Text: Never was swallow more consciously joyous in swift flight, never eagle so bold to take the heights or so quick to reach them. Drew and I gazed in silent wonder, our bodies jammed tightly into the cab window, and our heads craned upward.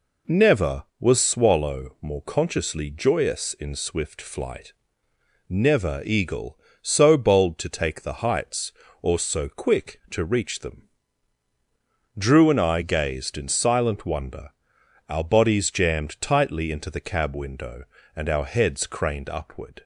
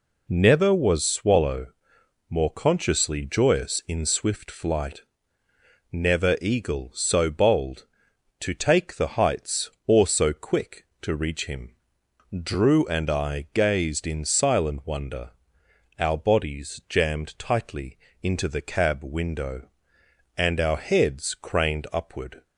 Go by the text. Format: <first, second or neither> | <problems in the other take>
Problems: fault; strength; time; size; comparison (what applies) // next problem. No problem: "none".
first | pauses between "swallow" and "more"; noticeable; at 1.6 s; 0.62 s long // says "him" for "them"; at 11.4 s // pauses between "tightly" and "into"; slight; at 17.9 s; 0.24 s long